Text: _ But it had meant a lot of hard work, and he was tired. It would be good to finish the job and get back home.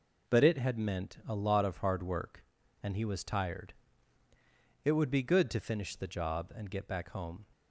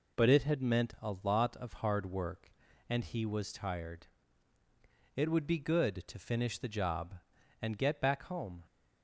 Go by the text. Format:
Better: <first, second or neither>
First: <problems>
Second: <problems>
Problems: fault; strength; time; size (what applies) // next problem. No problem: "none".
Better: neither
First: none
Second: none